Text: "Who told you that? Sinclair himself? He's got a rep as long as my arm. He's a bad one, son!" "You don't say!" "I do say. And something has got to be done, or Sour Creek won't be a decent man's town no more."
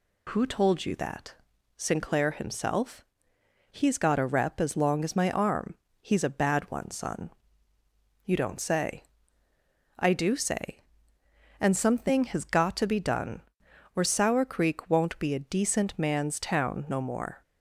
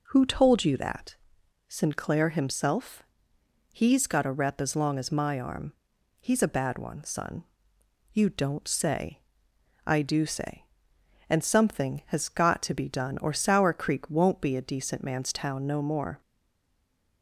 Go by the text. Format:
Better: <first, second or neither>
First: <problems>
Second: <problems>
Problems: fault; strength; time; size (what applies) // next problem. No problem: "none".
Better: first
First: none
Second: stays silent after the last word; from 16.2 s on; 1.0 s long